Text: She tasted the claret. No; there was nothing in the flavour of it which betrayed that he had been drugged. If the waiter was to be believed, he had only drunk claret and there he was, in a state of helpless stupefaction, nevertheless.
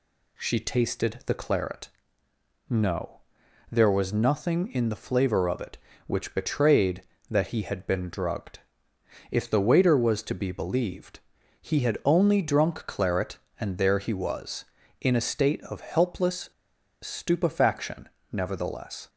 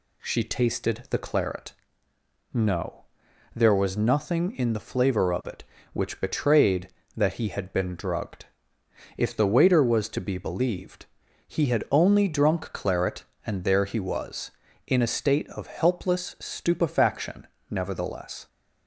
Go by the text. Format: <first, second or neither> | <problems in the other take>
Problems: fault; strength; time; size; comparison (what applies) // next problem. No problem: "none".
second | pauses between "helpless" and "stupefaction"; noticeable; at 16.5 s; 0.50 s long